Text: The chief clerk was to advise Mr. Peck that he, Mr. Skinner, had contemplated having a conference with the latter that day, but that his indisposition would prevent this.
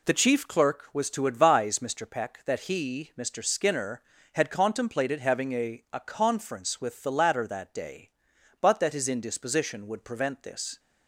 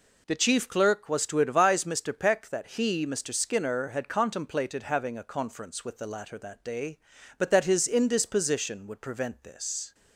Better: second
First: says "a" twice; at 5.9 s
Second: none

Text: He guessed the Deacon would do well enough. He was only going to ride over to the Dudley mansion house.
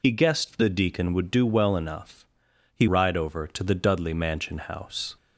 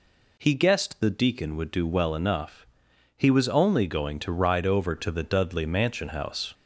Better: second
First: skips "was only going to"; at 2.8 s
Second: none

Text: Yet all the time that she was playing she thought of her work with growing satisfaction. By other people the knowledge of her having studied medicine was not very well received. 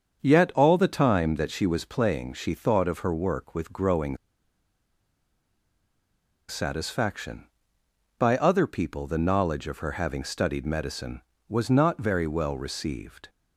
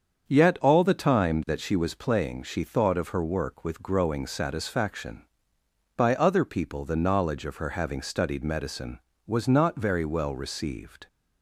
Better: second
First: starts louder than the rest; strong; until 1.2 s; 7 dB // pauses between "growing" and "satisfaction"; strong; at 4.1 s; 2.3 s long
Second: starts louder than the rest; strong; until 1.2 s; 7 dB

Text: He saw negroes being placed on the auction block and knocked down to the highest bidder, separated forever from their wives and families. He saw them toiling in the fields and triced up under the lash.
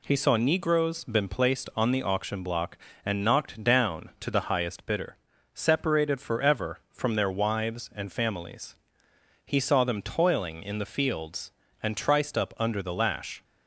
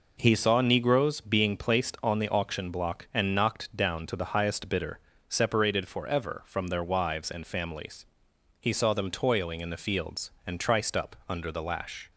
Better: second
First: says "been" for "being"; at 1.0 s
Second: none

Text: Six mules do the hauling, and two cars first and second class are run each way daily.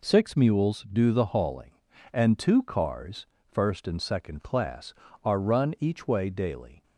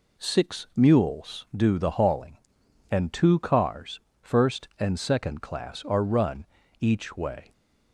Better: first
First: pauses between "cars" and "first"; slight; at 3.2 s; 0.24 s long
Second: pauses between "cars" and "first"; slight; at 3.9 s; 0.20 s long // pauses between "run" and "each"; slight; at 6.4 s; 0.36 s long // stops before "daily"; at 7.5 s

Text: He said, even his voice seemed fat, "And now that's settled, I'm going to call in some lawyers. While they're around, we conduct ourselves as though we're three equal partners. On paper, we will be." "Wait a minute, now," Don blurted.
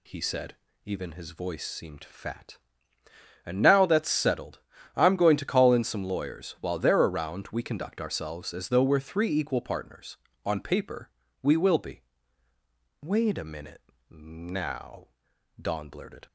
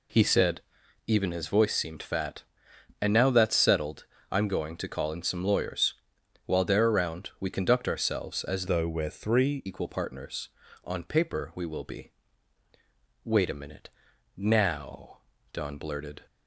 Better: first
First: none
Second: changes voice from "though" to "three"; from 8.6 to 9.6 s; 1.0 s long

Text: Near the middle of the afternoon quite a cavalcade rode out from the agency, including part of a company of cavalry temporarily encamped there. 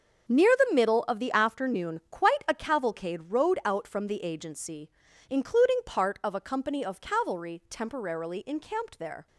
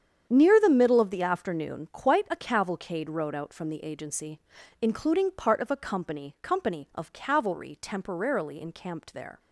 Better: first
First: starts louder than the rest; until 1.3 s; 7 dB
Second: starts louder than the rest; strong; until 1.3 s; 8.5 dB // says "company" twice; at 6.4 s

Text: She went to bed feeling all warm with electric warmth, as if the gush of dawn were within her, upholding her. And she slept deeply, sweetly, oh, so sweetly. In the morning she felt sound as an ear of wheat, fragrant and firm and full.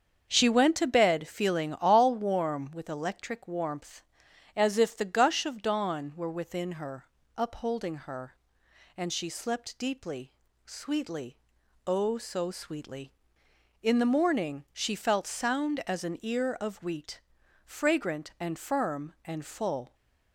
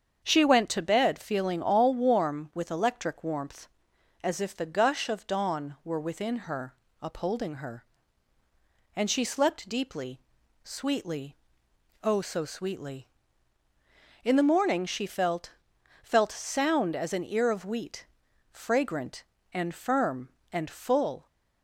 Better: first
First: starts louder than the rest; until 1.3 s; 7 dB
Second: starts louder than the rest; strong; until 1.2 s; 7.5 dB // says "felt" twice; at 16.0 s

